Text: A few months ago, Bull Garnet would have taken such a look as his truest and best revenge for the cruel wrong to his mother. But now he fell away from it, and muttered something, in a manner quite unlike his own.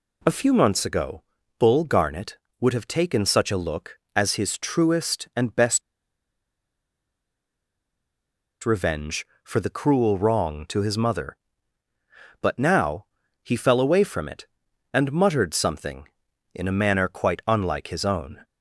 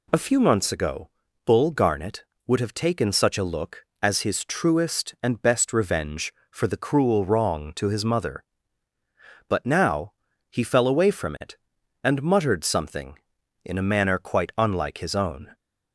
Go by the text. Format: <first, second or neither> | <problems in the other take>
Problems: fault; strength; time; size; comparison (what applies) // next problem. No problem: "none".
second | pauses between "best" and "revenge"; strong; at 5.8 s; 2.8 s long // pauses between "now" and "he"; slight; at 13.0 s; 0.36 s long; slight in the second